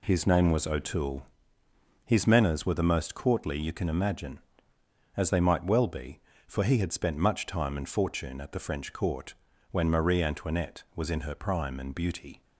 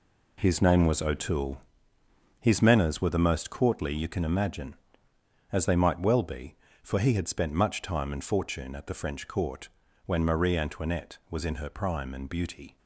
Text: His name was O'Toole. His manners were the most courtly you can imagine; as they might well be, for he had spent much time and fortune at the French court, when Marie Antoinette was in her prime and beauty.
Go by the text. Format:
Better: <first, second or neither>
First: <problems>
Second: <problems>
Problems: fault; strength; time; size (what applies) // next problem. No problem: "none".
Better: first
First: none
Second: gets quieter; strong; throughout; 9 dB